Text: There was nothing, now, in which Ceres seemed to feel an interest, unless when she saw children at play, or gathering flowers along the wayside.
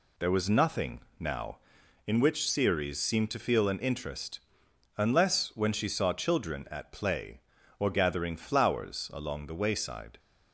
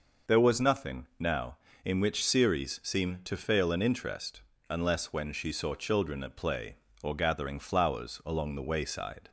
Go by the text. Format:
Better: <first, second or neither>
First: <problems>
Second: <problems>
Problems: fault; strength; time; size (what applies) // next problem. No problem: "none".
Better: first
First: none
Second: says "fail" for "feel"; at 3.3 s